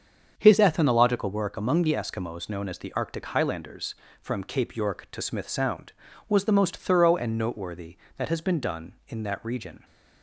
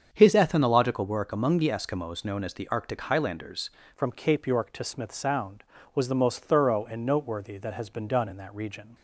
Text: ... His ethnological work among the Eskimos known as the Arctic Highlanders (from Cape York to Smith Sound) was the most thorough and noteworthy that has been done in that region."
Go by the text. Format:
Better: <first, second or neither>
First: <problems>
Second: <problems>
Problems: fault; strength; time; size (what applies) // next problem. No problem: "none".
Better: first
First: starts louder than the rest; until 1.3 s; 7 dB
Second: starts louder than the rest; until 1.1 s; 7 dB // changes voice at "from"; from 3.9 s on; 5.0 s long